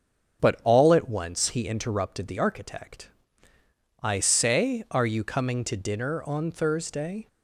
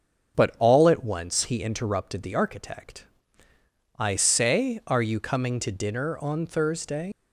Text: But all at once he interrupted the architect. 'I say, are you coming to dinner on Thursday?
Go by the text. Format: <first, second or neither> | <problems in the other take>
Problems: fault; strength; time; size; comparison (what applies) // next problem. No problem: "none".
first | starts louder than the rest; strong; until 1.4 s; 7 dB; strong in the first // leaves "Thursday" unfinished; at 7.1 s; 100 ms